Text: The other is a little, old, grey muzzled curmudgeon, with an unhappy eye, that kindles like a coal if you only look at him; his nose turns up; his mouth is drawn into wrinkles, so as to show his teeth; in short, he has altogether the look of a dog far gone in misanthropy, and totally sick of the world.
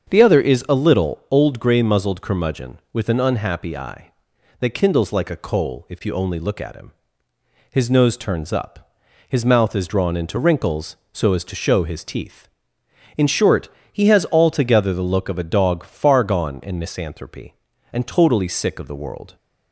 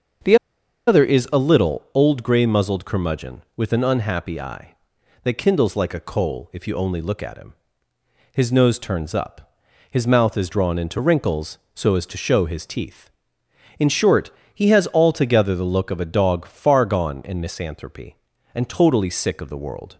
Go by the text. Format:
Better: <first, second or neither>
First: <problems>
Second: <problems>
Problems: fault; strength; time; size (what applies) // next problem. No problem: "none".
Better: first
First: starts louder than the rest; strong; until 1.1 s; 7 dB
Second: starts louder than the rest; until 1.7 s; 7 dB // pauses between "The" and "other"; noticeable; at 0.3 s; 0.51 s long